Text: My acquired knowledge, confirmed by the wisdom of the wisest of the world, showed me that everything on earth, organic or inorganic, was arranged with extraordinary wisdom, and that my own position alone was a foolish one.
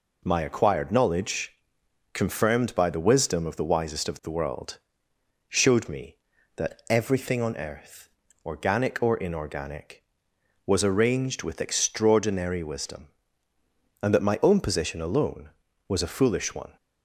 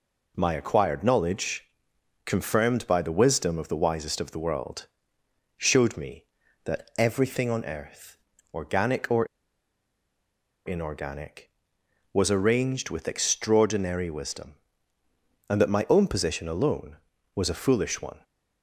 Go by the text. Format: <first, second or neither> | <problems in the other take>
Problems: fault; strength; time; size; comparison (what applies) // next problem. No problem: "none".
first | pauses between "or" and "inorganic"; strong; at 9.2 s; 1.4 s long